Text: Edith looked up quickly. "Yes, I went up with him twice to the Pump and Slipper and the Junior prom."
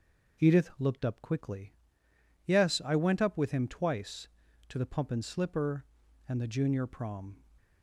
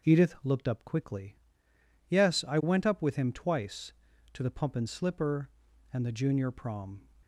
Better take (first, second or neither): neither